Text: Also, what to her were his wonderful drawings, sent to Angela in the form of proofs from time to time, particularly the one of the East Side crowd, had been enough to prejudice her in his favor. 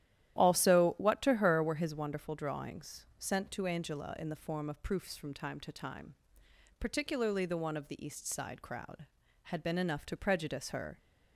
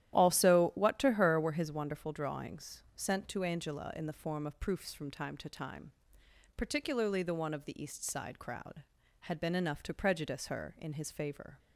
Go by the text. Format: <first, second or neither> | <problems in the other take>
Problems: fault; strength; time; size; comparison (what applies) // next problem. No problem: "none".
second | starts louder than the rest; strong; until 1.4 s; 12.5 dB; strong in the second // stops before "in his favor"; at 10.9 s